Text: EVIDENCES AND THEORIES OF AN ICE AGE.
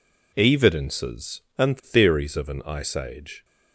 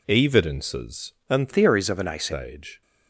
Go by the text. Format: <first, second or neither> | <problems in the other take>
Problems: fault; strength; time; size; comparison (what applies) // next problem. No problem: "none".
first | changes voice from "THEORIES" to "ICE"; from 1.5 to 2.3 s; 0.8 s long